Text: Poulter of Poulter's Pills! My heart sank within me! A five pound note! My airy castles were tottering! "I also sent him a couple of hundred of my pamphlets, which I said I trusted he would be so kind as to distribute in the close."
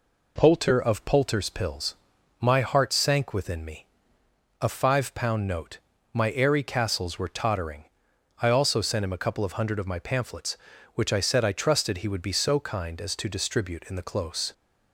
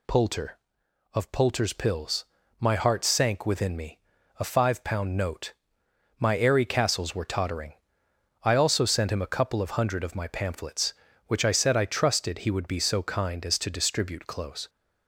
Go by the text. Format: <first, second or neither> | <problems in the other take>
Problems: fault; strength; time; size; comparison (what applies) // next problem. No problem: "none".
first | skips "in the"; at 14.2 s